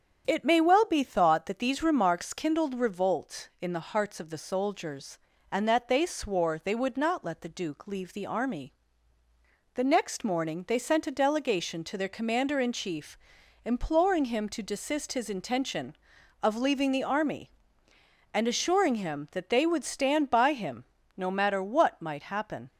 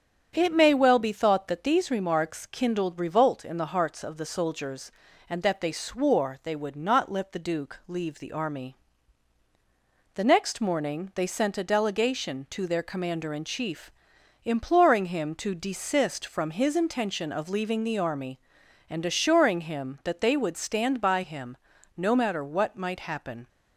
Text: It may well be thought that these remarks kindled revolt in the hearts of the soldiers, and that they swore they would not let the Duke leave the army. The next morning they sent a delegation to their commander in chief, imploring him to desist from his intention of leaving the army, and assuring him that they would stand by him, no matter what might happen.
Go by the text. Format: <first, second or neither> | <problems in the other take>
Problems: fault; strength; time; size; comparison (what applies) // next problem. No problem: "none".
second | starts louder than the rest; strong; until 1.2 s; 8 dB; strong in the second // skips "from"; at 15.1 s